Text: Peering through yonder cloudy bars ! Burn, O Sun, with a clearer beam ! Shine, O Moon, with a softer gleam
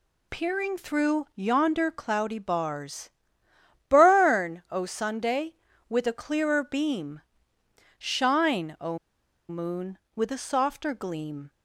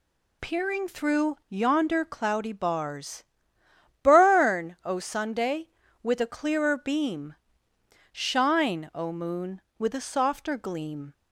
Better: second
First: pauses between "O" and "Moon"; noticeable; at 8.9 s; 0.51 s long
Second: none

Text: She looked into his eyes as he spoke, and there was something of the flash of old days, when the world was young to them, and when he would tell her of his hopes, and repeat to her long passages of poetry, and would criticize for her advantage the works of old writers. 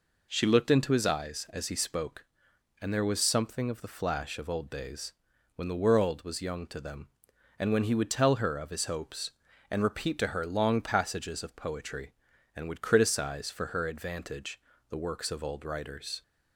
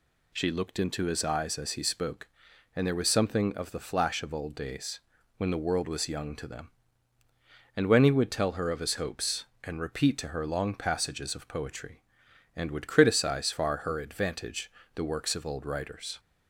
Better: first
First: pauses between "advantage" and "the"; slight; at 14.6 s; 0.30 s long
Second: says "far" for "for"; at 13.5 s // pauses between "advantage" and "the"; slight; at 14.7 s; 0.24 s long

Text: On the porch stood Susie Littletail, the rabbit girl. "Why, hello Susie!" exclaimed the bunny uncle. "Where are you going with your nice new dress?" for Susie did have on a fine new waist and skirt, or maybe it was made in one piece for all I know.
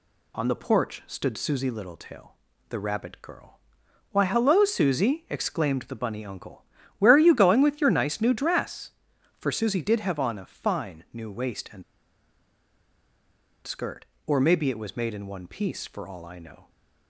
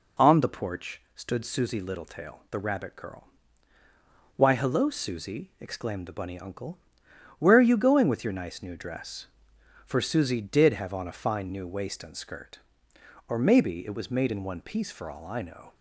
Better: second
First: pauses between "and" and "skirt"; strong; at 11.8 s; 1.8 s long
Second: none

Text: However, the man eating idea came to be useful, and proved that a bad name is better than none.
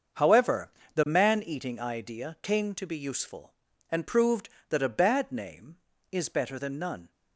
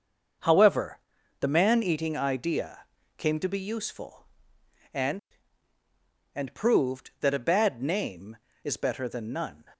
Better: first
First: starts louder than the rest; until 1.4 s; 6.5 dB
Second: starts louder than the rest; until 1.8 s; 6.5 dB // pauses between "idea" and "came"; slight; at 2.8 s; 0.34 s long // says "and" twice; at 6.3 s

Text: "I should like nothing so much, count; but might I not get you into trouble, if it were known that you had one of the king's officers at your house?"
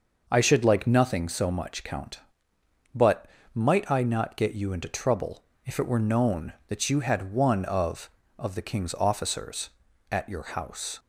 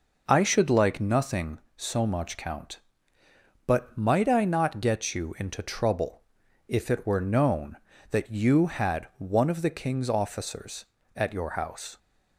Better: second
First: pauses between "but" and "might"; slight; at 3.2 s; 0.26 s long // says "of" twice; at 8.3 s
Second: none

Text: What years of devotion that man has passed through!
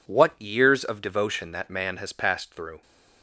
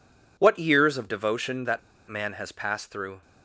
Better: first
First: none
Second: pauses between "that" and "man"; slight; at 1.7 s; 0.29 s long

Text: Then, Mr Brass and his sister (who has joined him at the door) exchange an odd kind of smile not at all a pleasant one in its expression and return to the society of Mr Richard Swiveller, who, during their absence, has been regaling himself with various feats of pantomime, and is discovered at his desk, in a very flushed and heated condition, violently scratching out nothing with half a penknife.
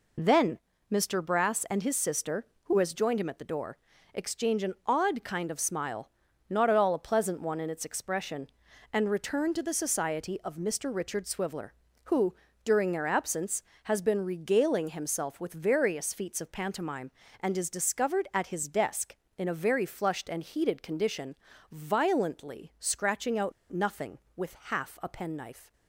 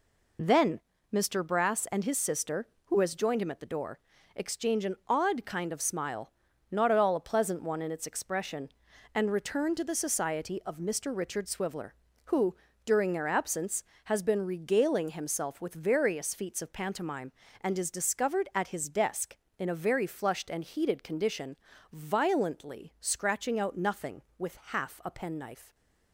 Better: second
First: pauses between "smile" and "not"; at 6.1 s; 0.38 s long // pauses between "out" and "nothing"; slight; at 23.5 s; 0.20 s long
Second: pauses between "smile" and "not"; at 6.3 s; 0.38 s long

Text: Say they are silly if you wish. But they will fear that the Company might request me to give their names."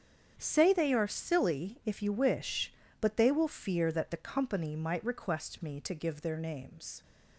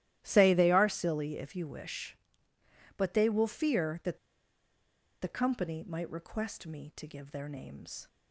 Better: first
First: starts louder than the rest; strong; until 1.3 s; 8 dB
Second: starts louder than the rest; strong; until 1.2 s; 13.5 dB // pauses between "that" and "the"; at 4.1 s; 1.0 s long

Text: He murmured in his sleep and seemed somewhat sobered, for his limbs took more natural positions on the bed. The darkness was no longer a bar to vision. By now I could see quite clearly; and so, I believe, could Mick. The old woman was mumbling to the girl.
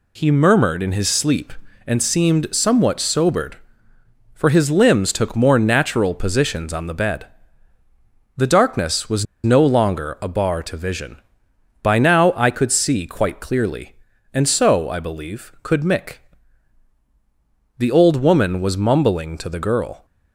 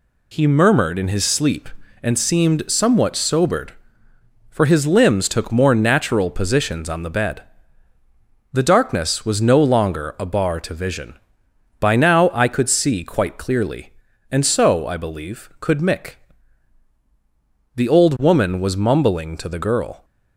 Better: second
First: pauses between "was" and "no"; slight; at 9.2 s; 0.19 s long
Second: none

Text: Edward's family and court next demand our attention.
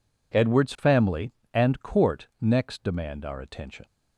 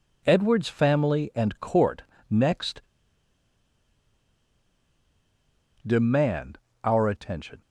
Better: first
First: none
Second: pauses between "court" and "next"; slight; at 2.0 s; 0.26 s long // pauses between "next" and "demand"; strong; at 2.8 s; 3.0 s long // pauses between "demand" and "our"; slight; at 6.5 s; 0.26 s long

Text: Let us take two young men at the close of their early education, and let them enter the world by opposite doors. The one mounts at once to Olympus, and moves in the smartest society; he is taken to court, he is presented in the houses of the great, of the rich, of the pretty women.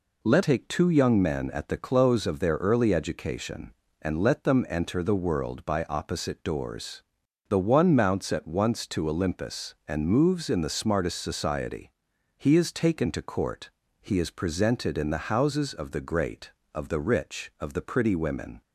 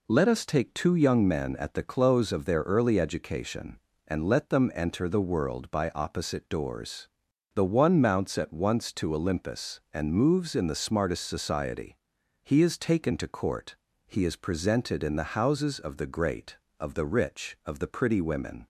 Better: second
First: skips "us"; at 0.4 s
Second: none

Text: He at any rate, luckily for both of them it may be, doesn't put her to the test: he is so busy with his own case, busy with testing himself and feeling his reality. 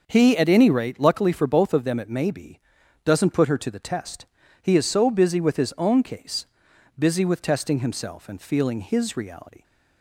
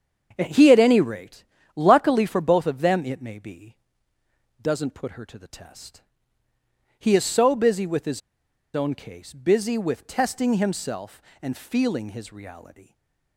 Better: first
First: starts louder than the rest; noticeable; until 1.0 s; 6 dB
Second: starts louder than the rest; strong; until 1.3 s; 7.5 dB // pauses between "his" and "own"; noticeable; at 8.2 s; 0.55 s long // stays silent after the last word; slight; from 12.8 s on; 0.5 s long

